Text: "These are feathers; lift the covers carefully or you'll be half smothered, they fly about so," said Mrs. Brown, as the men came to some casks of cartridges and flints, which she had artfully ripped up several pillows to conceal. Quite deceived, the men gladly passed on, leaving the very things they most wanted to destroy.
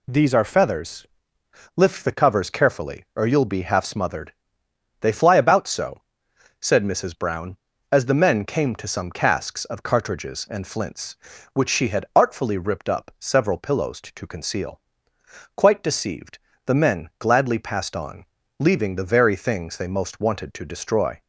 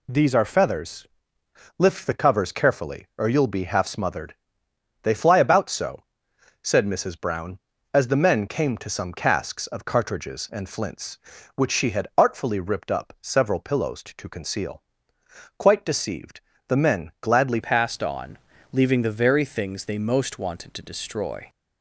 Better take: first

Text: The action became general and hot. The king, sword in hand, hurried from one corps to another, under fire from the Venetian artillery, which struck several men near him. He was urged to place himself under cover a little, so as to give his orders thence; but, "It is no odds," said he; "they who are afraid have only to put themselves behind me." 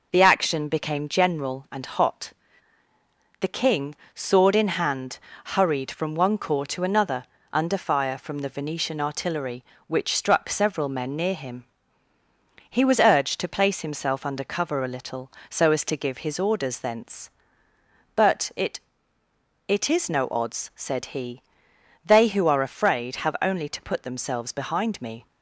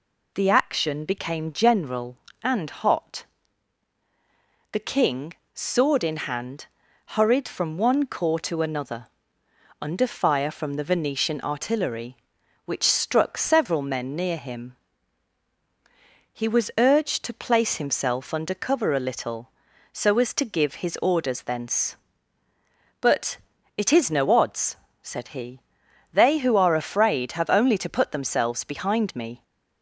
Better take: second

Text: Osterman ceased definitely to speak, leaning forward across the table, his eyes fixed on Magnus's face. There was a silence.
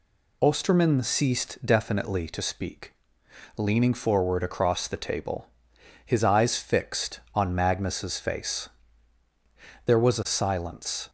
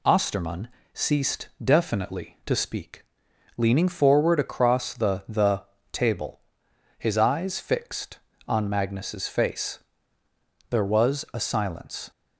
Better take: first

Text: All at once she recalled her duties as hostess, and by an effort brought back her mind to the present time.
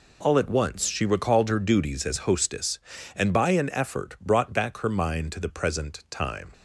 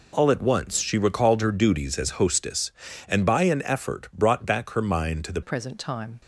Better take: first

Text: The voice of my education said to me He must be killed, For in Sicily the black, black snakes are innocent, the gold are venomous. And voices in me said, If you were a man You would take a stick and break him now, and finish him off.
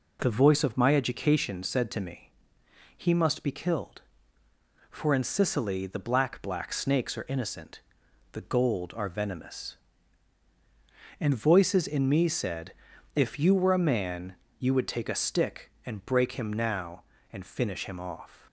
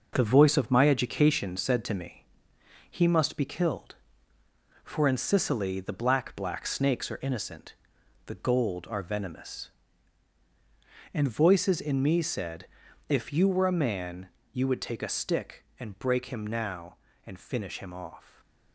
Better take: first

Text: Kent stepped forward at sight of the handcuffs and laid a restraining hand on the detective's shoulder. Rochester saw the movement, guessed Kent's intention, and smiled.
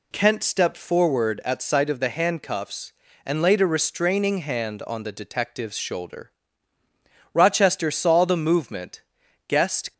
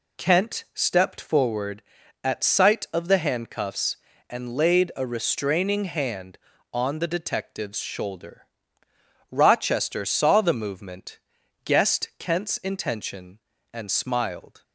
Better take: second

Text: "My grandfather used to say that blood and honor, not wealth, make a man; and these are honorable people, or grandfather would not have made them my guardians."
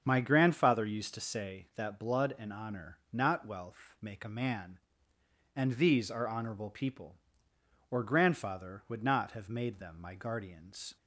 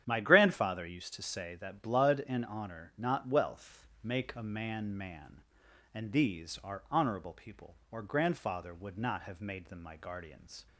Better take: first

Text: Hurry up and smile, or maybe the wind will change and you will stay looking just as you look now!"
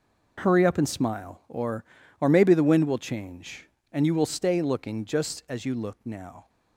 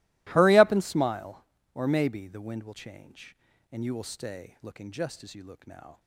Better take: second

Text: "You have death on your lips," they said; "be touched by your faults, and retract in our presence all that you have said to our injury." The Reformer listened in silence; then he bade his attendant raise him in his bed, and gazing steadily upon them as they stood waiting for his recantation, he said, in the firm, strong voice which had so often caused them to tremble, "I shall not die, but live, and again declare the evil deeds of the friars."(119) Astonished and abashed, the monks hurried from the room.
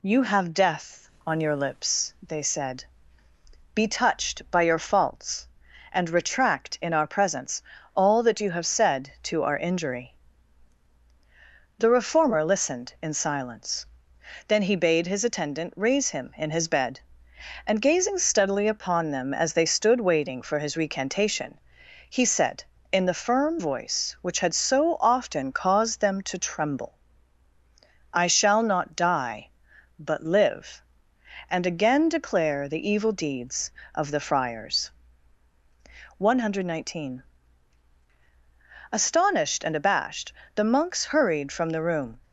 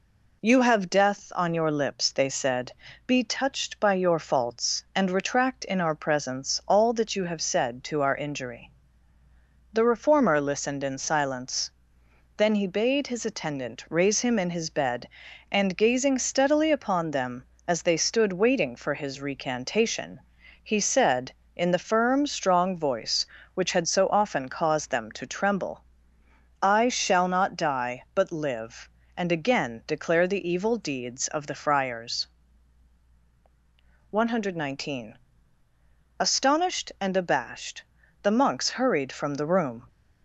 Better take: second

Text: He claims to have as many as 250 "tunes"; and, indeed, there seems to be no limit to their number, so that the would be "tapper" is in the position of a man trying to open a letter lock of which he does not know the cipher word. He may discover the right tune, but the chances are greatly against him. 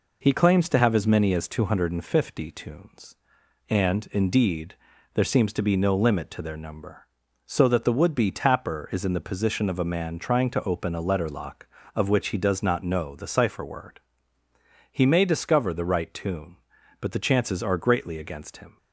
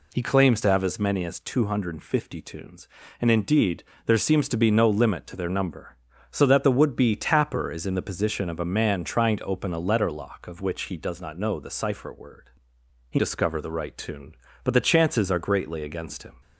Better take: first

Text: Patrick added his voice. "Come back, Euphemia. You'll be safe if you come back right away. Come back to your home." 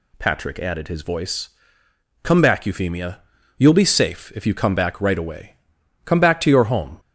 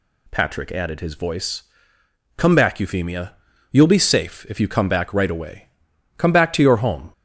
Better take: neither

